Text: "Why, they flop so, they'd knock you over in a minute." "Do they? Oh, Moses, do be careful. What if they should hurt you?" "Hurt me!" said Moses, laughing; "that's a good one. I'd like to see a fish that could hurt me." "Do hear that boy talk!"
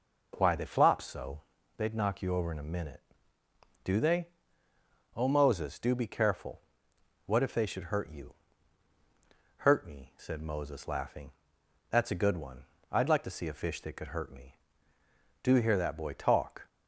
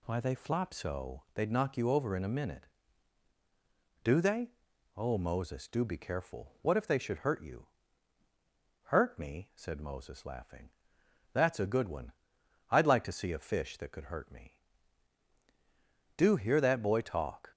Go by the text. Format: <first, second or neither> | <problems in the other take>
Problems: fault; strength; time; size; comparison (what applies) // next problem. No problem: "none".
neither | none